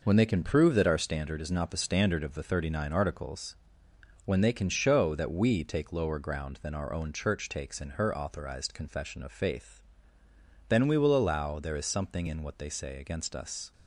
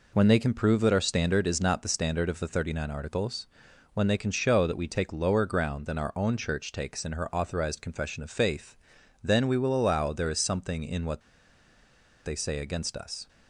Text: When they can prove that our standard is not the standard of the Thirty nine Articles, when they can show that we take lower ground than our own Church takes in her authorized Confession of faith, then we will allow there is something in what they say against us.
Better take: first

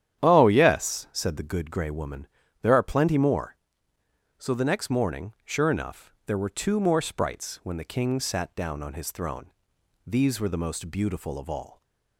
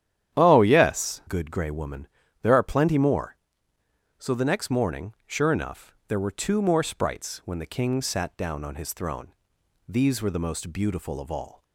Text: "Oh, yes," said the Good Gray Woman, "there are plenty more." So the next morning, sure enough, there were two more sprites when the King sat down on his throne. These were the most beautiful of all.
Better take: first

